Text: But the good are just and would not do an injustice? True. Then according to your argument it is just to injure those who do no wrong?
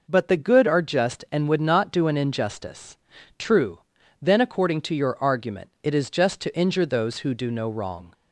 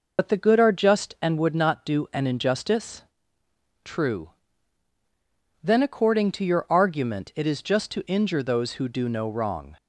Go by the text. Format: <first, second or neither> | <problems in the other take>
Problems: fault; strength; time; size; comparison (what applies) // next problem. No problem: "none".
first | loses the start of "But"; at 0.1 s; 65 ms